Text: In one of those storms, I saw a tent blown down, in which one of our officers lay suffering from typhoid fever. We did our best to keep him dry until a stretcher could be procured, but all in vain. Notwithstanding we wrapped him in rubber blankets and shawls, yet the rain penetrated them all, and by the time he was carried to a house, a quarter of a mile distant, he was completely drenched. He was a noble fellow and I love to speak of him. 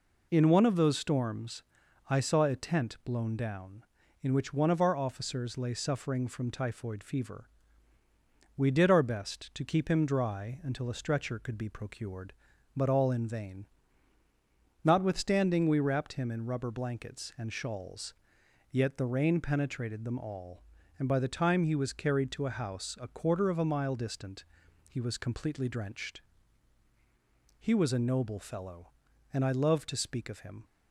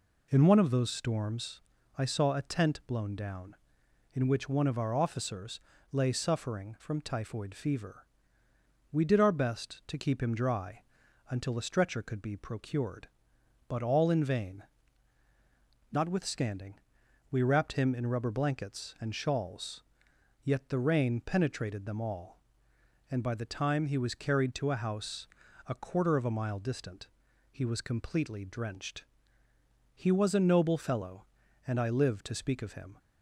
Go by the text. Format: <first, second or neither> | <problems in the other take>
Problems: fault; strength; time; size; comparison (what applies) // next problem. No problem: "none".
first | pauses between "officers" and "lay"; slight; at 5.5 s; 0.32 s long // pauses between "dry" and "until"; noticeable; at 10.8 s; 0.48 s long // pauses between "Notwithstanding" and "we"; noticeable; at 16.7 s; 0.56 s long // says "live" for "love"; at 31.9 s